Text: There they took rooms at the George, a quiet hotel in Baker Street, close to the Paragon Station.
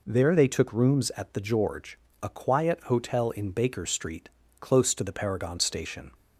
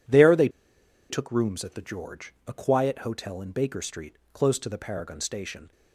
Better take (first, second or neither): first